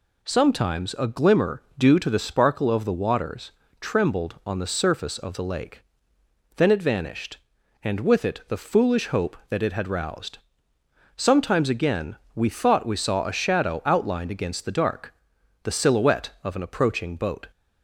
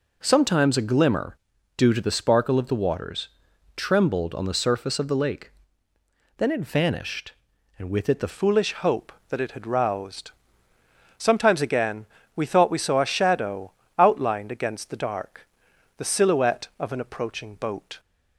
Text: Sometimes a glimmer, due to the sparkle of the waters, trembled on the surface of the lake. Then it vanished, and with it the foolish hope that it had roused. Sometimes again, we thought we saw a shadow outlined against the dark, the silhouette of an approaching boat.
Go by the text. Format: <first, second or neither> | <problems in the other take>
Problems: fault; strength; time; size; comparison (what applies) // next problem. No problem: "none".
first | changes voice at "foolish"; from 8.2 s on; 9.7 s long // pauses between "shadow" and "outlined"; slight; at 13.7 s; 0.26 s long